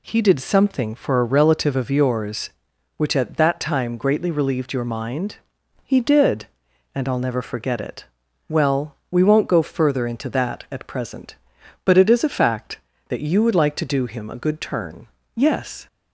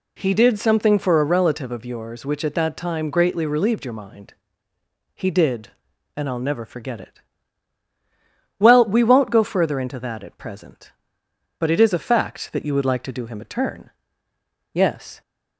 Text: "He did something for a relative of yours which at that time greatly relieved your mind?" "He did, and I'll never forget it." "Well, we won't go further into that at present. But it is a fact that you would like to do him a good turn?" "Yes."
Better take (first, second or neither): first